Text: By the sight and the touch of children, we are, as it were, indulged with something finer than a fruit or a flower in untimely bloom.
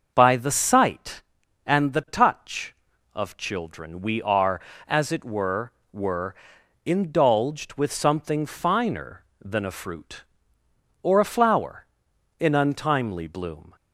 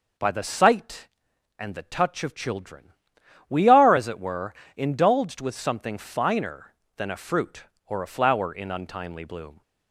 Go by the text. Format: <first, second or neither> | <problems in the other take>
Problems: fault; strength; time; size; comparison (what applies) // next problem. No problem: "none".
second | starts louder than the rest; until 1.1 s; 6.5 dB // says "were" twice; at 5.9 s